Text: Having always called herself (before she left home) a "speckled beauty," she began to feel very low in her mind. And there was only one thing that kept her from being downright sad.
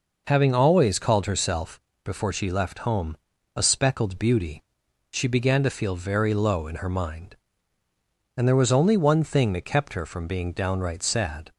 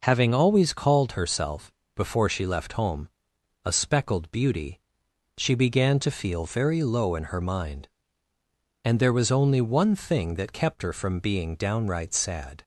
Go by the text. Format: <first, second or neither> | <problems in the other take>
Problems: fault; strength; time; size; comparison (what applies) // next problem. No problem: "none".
neither | none